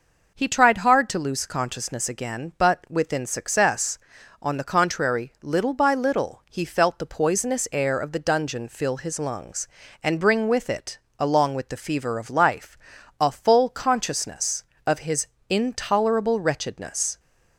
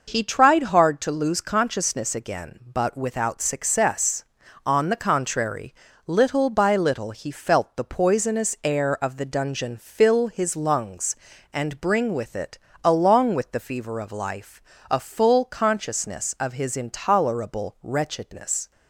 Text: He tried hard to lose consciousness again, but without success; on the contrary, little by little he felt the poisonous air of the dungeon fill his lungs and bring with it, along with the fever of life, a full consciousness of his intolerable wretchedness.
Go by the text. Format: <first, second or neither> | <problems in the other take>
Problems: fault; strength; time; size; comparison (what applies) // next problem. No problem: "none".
second | says "within" for "without"; at 2.8 s // pauses between "his" and "intolerable"; slight; at 15.2 s; 0.22 s long